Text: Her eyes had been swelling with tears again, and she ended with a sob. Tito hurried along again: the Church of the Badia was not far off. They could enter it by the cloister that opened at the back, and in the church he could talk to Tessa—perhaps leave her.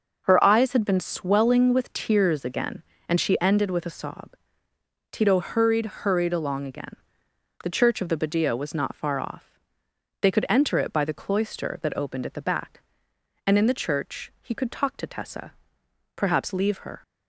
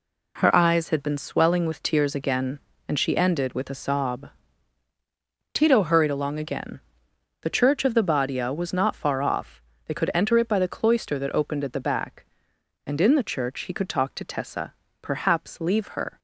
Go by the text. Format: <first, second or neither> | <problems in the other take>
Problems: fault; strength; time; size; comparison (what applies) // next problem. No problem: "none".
second | says "hurried" twice; at 5.8 s